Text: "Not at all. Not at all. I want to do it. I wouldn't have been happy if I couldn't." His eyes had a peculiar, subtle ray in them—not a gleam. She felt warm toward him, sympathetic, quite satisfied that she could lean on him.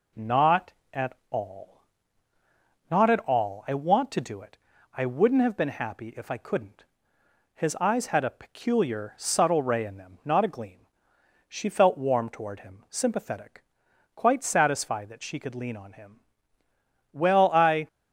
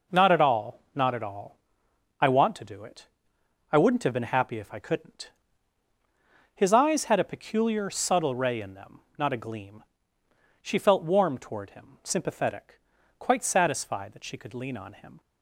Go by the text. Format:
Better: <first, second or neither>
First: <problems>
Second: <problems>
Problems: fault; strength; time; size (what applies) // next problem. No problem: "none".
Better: second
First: goes on to say "Well I"; noticeable; from 17.1 s on; 0.76 s long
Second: none